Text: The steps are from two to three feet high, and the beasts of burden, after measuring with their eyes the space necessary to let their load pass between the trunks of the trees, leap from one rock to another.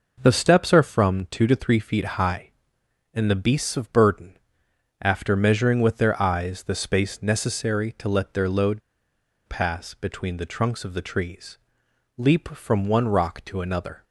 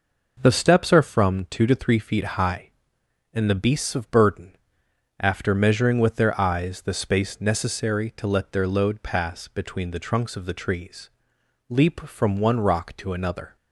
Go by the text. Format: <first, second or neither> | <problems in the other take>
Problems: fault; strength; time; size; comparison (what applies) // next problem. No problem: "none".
second | pauses between "load" and "pass"; noticeable; at 8.8 s; 0.66 s long